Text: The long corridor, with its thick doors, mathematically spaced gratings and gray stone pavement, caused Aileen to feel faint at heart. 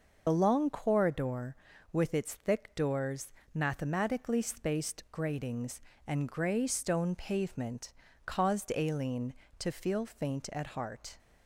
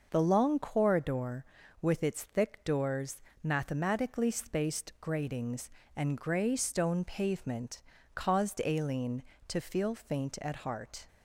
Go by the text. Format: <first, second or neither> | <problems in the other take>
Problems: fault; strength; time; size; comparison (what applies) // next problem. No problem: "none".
second | loses the start of "The"; at 0.2 s; 45 ms